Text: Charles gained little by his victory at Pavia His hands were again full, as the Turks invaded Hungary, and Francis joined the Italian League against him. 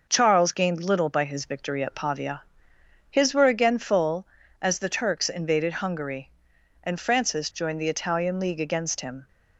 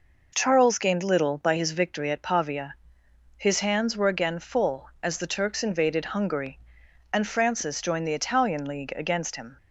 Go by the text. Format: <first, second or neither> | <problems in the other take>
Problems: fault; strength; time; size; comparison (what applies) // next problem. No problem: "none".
second | pauses between "Pavia" and "His"; noticeable; at 2.4 s; 0.70 s long; noticeable in the second // skips "hands"; at 3.3 s